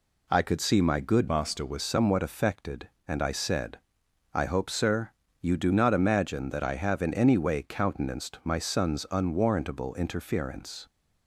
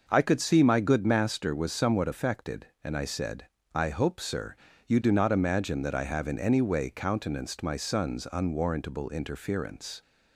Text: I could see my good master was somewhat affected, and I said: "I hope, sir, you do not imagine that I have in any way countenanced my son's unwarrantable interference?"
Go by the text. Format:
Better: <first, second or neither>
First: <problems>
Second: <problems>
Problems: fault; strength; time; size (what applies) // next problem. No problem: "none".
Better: second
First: changes voice from "master" to "was"; from 1.2 to 1.8 s; 0.6 s long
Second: none